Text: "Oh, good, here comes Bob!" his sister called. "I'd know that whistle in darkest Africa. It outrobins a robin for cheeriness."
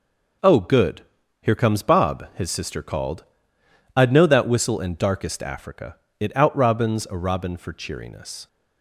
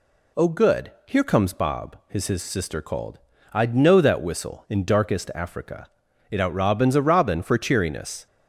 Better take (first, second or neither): first